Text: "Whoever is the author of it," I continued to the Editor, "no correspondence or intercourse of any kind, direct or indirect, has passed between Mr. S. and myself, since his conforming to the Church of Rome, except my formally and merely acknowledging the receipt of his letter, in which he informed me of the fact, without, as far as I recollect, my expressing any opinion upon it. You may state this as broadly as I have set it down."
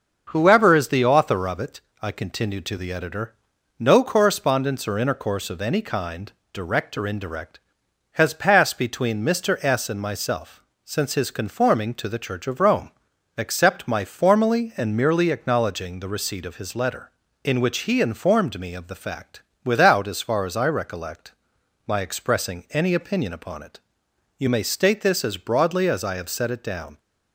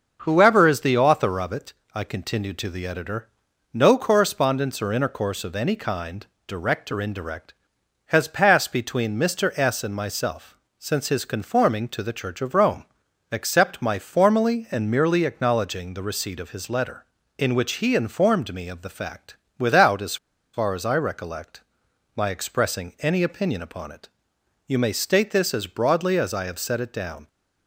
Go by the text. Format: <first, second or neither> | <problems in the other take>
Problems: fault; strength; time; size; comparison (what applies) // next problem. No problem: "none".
first | starts louder than the rest; noticeable; until 1.2 s; 6 dB; noticeable in the first // pauses between "as" and "far"; at 20.1 s; 0.36 s long